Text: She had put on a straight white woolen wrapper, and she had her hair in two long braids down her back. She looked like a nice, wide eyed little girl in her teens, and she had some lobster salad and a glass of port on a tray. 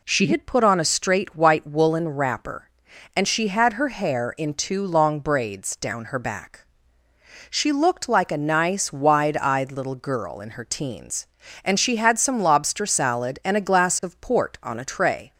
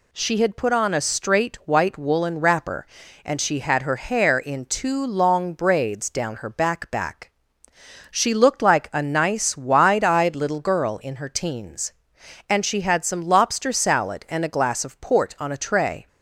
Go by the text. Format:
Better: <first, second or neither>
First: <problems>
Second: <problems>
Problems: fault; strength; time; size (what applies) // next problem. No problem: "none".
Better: first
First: none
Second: says "back" twice; at 6.9 s